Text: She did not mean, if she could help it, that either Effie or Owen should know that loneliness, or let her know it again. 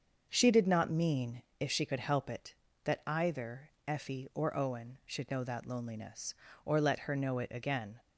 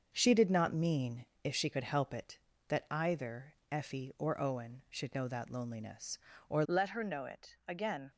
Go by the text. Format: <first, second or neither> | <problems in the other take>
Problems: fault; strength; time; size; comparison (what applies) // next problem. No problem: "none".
first | starts louder than the rest; until 1.1 s; 6.5 dB; also in the first // pauses between "either" and "Effie"; slight; at 3.5 s; 0.16 s long; slight in the first // changes voice at "let"; from 6.6 s on; 1.5 s long